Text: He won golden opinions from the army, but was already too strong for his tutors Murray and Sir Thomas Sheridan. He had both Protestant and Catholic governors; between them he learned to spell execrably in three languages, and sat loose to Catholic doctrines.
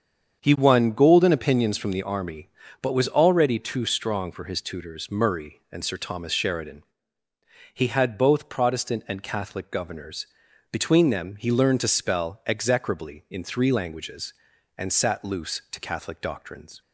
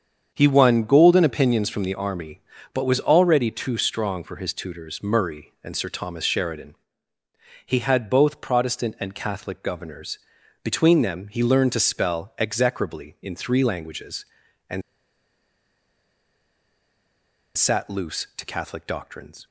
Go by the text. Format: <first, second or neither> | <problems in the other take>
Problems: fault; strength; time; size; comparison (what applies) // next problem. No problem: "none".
first | starts louder than the rest; strong; until 1.3 s; 7.5 dB; strong in the first // pauses between "and" and "sat"; strong; at 14.8 s; 2.7 s long